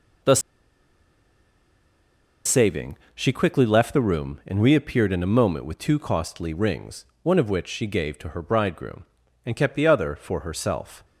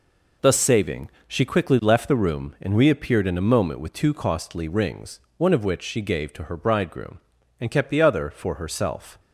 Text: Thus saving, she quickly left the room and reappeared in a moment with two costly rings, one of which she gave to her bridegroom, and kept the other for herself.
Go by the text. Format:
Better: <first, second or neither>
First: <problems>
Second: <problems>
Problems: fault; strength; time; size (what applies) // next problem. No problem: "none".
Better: second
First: pauses between "Thus" and "saving"; strong; at 0.3 s; 2.0 s long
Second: none